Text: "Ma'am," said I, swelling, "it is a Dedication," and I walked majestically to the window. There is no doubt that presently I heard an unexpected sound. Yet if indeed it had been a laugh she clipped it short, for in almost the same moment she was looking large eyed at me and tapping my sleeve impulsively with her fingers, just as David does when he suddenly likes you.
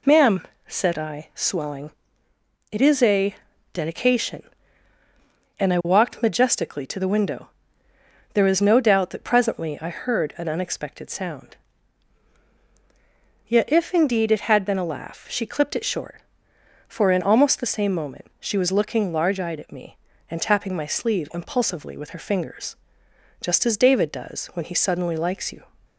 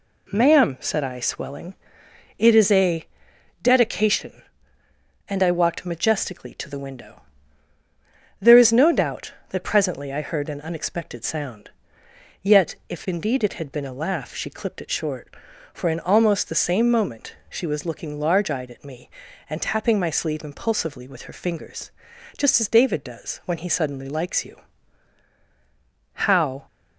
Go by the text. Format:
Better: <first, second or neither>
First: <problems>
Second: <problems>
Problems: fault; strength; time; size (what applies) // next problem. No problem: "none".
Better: first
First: pauses between "a" and "Dedication"; at 3.3 s; 0.40 s long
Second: pauses between "a" and "Dedication"; noticeable; at 3.0 s; 0.56 s long // goes on to say "How"; from 26.1 s on; 0.54 s long